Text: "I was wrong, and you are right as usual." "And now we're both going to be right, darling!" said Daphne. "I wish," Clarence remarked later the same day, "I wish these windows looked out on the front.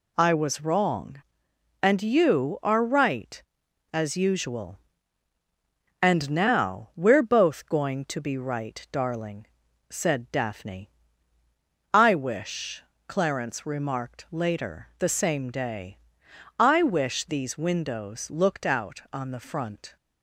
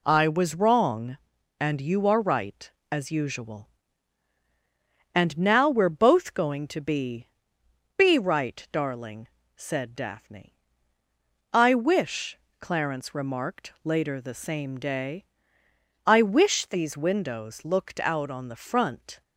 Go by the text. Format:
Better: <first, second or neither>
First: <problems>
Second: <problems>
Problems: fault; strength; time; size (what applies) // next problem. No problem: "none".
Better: first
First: none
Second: says "be" twice; at 7.9 s